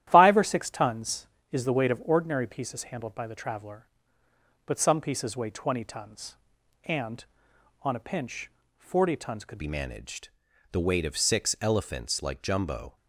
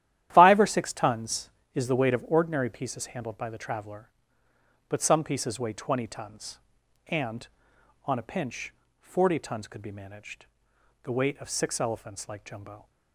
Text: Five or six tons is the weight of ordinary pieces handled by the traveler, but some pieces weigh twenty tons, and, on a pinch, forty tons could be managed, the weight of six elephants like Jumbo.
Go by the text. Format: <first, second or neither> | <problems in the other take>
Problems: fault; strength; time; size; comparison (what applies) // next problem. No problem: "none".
second | starts louder than the rest; strong; until 1.1 s; 12 dB; strong in the second // changes voice at "be"; from 9.5 s on; 3.4 s long